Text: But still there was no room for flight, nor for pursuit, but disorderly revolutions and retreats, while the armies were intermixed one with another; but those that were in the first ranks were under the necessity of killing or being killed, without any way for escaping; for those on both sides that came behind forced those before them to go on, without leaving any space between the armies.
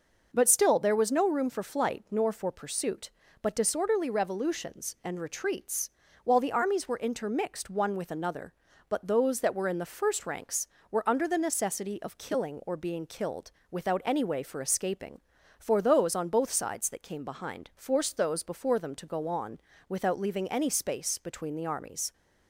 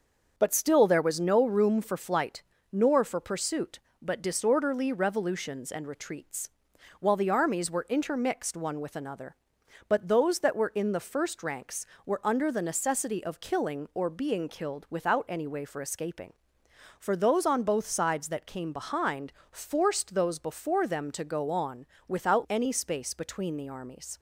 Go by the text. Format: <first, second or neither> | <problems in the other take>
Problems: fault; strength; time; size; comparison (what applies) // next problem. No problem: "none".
first | starts louder than the rest; until 1.3 s; 6.5 dB // pauses between "behind" and "forced"; slight; at 19.3 s; 0.20 s long // skips "leaving"; at 22.4 s